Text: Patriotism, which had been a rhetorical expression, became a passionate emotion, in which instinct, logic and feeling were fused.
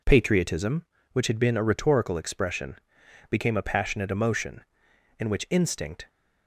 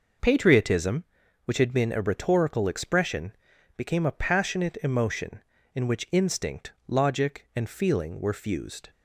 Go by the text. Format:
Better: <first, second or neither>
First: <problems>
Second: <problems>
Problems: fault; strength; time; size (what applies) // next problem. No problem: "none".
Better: second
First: stops before "logic and feeling were fused"; at 6.0 s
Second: none